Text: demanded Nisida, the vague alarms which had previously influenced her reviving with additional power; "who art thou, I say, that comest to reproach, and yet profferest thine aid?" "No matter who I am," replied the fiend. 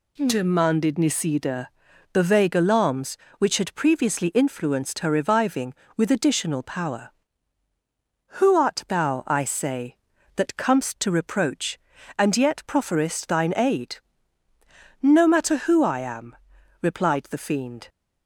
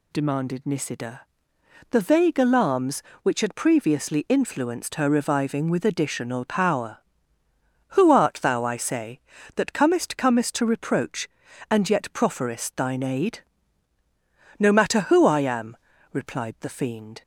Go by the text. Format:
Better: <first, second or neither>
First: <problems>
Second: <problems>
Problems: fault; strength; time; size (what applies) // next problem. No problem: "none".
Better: first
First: none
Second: says "comest" twice; at 10.1 s